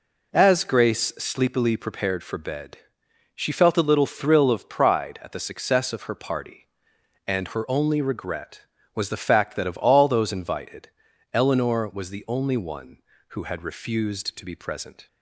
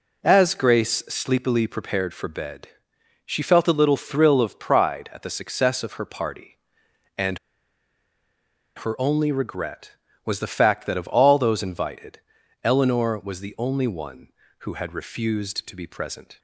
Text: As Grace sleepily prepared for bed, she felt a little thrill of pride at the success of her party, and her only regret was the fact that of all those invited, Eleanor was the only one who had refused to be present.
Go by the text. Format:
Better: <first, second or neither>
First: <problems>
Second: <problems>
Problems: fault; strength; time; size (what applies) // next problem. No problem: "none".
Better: first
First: none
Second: pauses between "and" and "her"; strong; at 7.3 s; 1.3 s long